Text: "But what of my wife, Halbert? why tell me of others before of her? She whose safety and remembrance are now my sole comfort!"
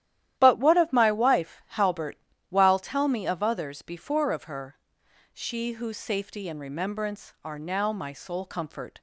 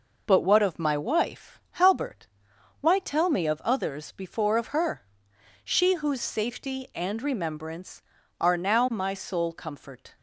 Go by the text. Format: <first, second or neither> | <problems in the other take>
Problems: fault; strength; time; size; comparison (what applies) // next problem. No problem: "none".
second | starts louder than the rest; strong; until 1.4 s; 12 dB // says "while" for "why"; at 2.4 s